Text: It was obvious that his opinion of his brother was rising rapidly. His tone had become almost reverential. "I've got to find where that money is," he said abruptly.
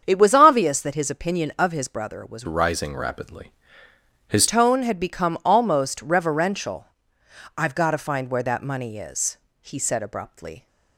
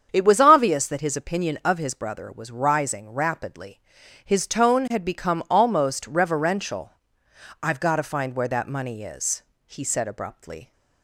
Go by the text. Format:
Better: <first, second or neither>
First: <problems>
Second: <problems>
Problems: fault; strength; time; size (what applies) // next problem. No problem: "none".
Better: second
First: starts louder than the rest; strong; until 1.0 s; 7.5 dB // changes voice from "rising" to "His"; from 2.4 to 4.4 s; 2.0 s long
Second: starts louder than the rest; strong; until 1.1 s; 7.5 dB